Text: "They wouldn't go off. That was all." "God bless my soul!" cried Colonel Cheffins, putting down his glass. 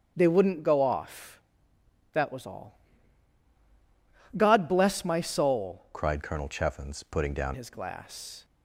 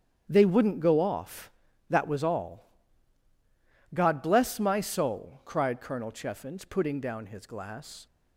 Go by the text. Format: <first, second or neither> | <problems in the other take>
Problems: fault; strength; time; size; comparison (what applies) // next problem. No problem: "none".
second | starts louder than the rest; strong; until 1.1 s; 8 dB; strong in the second // changes voice from "cried" to "down"; from 5.9 to 7.5 s; 1.6 s long